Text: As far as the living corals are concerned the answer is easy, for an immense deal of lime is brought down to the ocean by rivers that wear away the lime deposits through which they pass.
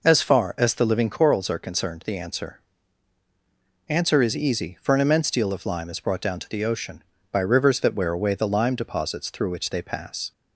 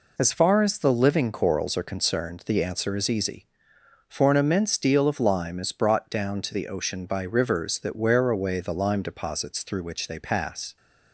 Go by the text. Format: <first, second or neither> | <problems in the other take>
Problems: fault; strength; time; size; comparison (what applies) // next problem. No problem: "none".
second | says "answer" twice; at 3.8 s